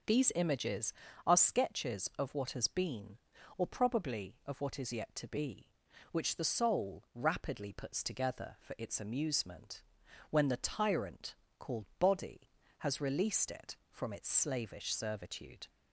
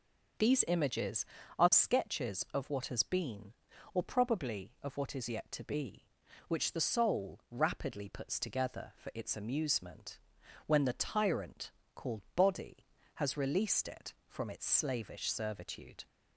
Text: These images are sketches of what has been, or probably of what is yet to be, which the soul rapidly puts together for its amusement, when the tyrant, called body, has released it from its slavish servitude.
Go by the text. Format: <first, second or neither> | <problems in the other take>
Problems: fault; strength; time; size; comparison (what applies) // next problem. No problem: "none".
neither | none